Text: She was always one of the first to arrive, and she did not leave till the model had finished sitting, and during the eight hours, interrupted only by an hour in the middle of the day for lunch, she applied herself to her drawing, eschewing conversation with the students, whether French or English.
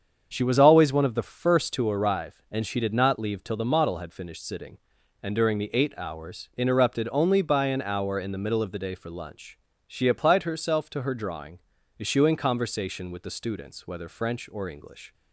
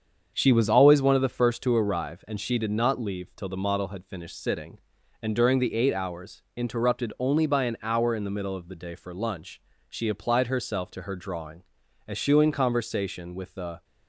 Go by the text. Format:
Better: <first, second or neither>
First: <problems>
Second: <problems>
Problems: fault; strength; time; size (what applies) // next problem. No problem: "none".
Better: first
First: starts louder than the rest; strong; until 1.3 s; 7 dB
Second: starts louder than the rest; strong; until 1.3 s; 7 dB // stops before "students whether French or English"; at 13.8 s